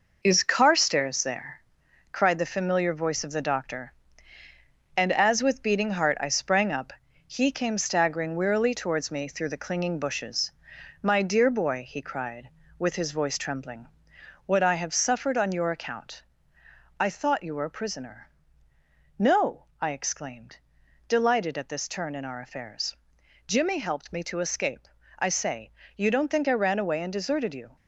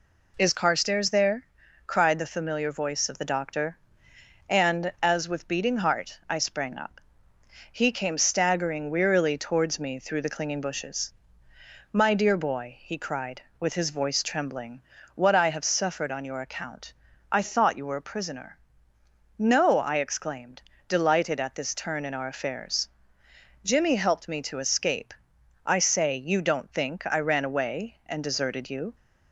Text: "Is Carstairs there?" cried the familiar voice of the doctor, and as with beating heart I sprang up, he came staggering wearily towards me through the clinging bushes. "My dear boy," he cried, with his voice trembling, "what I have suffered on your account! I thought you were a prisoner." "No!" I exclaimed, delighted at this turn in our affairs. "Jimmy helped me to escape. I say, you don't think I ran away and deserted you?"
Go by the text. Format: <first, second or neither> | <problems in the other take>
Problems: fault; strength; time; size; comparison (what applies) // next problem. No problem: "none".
second | gets quieter; throughout; 6.5 dB